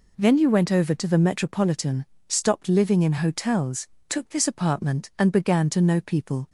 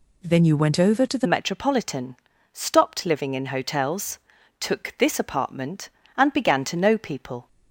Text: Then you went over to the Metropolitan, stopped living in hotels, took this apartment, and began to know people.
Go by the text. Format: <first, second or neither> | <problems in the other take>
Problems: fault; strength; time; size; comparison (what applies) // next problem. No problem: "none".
first | changes voice at "Metropolitan"; from 1.2 s on; 6.2 s long